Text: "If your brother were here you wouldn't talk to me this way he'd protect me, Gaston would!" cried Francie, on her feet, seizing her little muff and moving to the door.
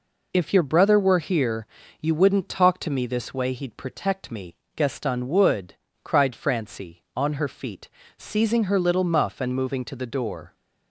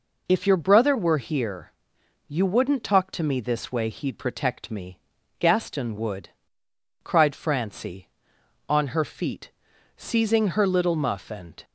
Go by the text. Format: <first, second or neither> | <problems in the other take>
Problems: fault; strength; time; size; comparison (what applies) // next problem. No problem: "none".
first | pauses between "here" and "you"; noticeable; at 1.6 s; 0.56 s long; slight in the first // stops before "moving to the door"; at 11.6 s